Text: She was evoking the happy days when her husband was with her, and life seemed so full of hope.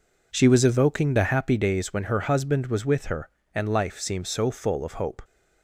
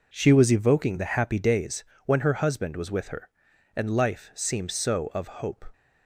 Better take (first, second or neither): first